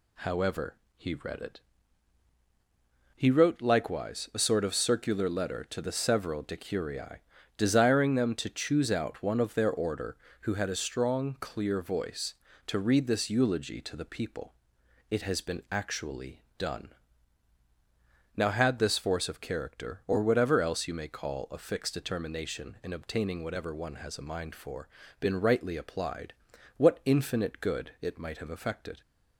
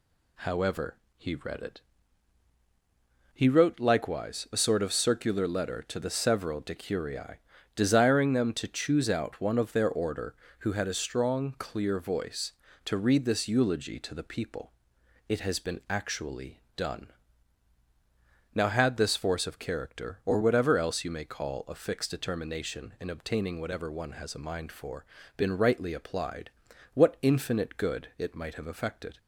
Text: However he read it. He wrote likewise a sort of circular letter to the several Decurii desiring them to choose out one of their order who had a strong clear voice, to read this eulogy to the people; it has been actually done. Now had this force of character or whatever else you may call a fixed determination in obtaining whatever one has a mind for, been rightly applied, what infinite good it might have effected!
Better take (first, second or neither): neither